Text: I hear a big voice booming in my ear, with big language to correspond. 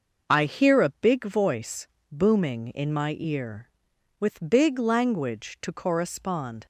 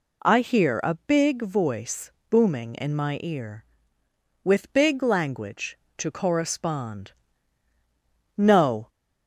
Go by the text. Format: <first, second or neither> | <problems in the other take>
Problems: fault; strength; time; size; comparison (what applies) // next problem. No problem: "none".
first | pauses between "voice" and "booming"; slight; at 2.1 s; 0.18 s long; slight in the first // goes on to say "No"; from 8.3 s on; 0.52 s long